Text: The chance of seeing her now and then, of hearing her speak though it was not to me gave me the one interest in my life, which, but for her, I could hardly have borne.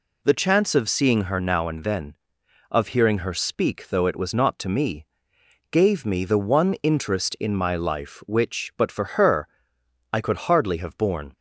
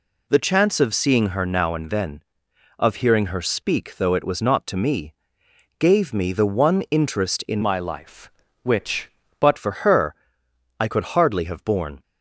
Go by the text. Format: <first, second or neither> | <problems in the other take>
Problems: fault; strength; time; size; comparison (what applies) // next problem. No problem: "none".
first | pauses between "me" and "gave"; noticeable; at 5.1 s; 0.66 s long; noticeable in the first // changes voice from "my" to "but"; from 7.6 to 9.5 s; 1.9 s long